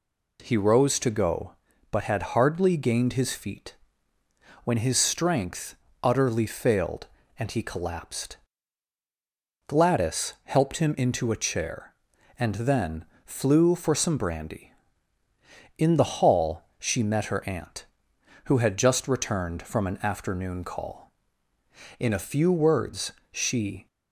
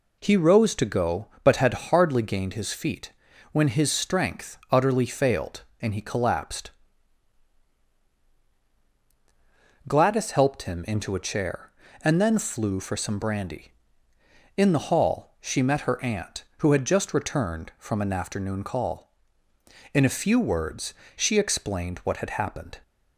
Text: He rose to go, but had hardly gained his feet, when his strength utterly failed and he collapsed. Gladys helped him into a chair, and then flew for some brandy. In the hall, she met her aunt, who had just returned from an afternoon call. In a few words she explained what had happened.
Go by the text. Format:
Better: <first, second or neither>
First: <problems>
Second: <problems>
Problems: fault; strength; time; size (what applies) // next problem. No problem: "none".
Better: second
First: pauses between "strength" and "utterly"; slight; at 5.7 s; 0.28 s long // pauses between "then" and "flew"; slight; at 13.0 s; 0.20 s long // pauses between "words" and "she"; slight; at 23.1 s; 0.18 s long // stops before "explained what had happened"; at 23.8 s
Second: pauses between "words" and "she"; slight; at 20.9 s; 0.24 s long